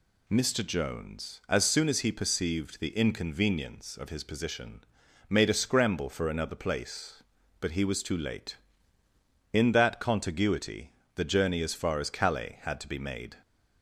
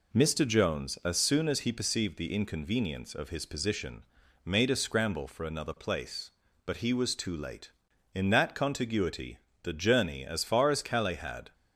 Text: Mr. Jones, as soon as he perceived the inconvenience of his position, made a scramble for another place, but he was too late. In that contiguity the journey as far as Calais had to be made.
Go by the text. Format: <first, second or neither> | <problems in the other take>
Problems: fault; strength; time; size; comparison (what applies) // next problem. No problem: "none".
first | pauses between "contiguity" and "the"; slight; at 9.3 s; 0.24 s long; slight in the first // stops before "to be made"; at 11.5 s